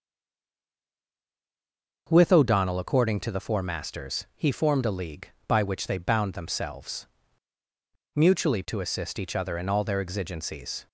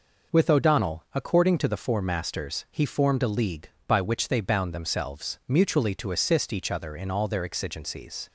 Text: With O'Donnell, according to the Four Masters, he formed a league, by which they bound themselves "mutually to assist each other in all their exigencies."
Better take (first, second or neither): second